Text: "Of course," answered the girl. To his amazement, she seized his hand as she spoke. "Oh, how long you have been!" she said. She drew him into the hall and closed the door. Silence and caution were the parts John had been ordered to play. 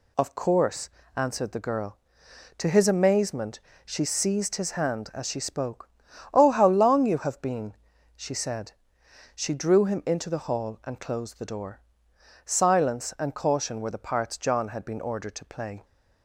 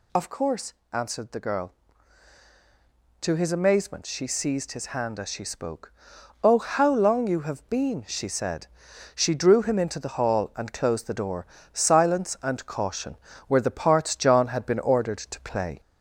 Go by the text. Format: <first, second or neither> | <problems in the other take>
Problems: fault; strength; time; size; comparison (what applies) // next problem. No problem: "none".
first | gets louder; slight; throughout; 2 dB